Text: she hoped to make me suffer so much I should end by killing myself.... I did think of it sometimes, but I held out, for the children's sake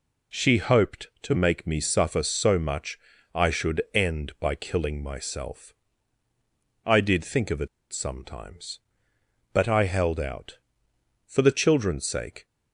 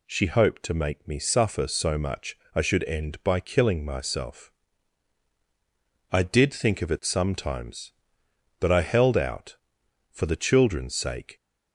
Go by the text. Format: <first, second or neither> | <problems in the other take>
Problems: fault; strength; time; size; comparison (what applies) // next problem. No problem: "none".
second | pauses between "much" and "I"; at 2.9 s; 0.38 s long; slight in the second // pauses between "it" and "sometimes"; slight; at 7.6 s; 0.25 s long